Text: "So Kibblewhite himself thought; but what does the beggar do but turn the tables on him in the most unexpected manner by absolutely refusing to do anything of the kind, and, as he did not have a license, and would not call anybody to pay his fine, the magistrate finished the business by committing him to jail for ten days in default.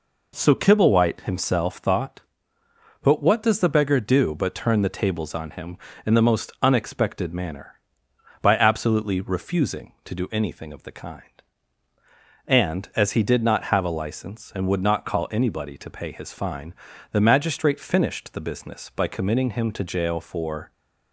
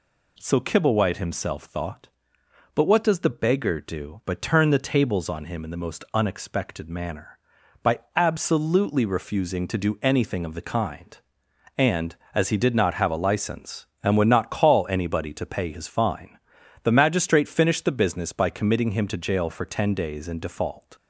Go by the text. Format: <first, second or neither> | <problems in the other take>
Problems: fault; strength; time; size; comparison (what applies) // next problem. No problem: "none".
second | stops before "ten days in default"; at 20.7 s